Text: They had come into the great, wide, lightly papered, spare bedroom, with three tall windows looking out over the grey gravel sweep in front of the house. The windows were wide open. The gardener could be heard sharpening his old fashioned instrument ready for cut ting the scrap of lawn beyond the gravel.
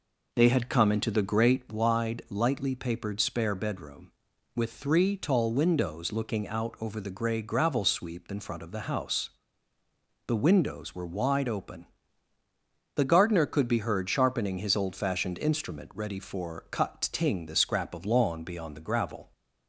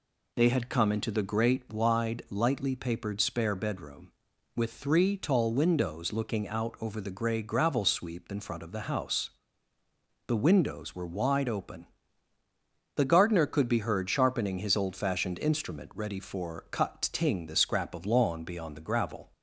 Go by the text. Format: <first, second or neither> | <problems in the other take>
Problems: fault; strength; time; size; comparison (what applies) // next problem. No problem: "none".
second | starts louder than the rest; noticeable; until 1.8 s; 4.5 dB